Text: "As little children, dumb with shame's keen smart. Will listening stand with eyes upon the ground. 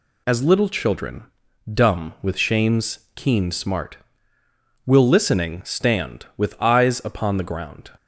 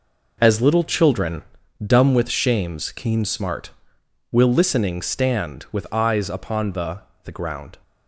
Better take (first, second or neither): first